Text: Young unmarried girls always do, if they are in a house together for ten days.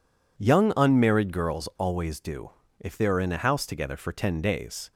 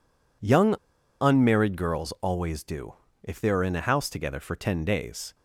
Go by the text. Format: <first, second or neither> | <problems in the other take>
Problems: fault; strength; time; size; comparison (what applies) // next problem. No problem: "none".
first | pauses between "Young" and "unmarried"; at 0.7 s; 0.44 s long